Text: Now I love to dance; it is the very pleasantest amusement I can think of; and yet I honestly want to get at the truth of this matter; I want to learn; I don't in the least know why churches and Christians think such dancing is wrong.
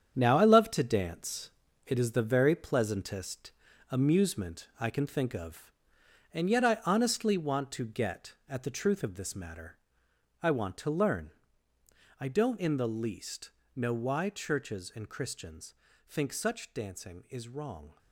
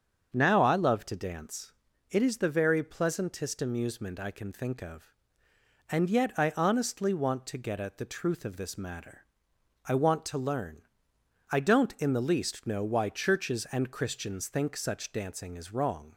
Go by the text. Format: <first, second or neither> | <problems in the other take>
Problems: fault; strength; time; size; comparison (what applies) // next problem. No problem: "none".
second | gets quieter; strong; throughout; 9 dB // starts louder than the rest; strong; until 1.1 s; 8 dB; also in the second // pauses between "pleasantest" and "amusement"; at 3.5 s; 0.40 s long // pauses between "least" and "know"; slight; at 13.5 s; 0.24 s long // pauses between "Christians" and "think"; slight; at 15.7 s; 0.34 s long